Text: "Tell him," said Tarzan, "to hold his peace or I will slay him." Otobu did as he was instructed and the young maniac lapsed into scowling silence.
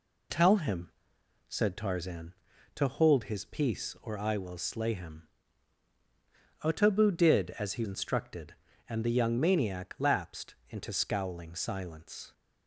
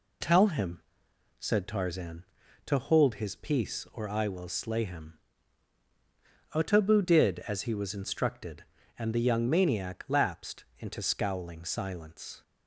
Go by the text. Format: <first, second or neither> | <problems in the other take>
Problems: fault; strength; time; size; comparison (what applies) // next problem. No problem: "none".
second | skips "was"; at 7.8 s